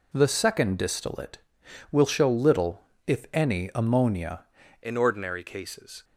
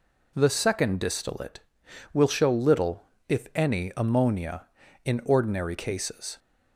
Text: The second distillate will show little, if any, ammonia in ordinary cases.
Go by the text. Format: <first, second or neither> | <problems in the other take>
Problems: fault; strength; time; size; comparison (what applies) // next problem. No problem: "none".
second | changes voice at "in"; from 4.8 s on; 1.2 s long